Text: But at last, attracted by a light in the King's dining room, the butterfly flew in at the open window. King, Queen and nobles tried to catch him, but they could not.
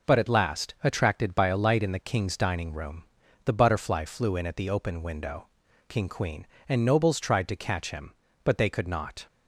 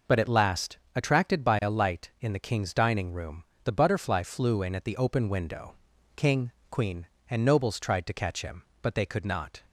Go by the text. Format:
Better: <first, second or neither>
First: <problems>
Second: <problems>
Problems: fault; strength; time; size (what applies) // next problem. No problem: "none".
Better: neither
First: none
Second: none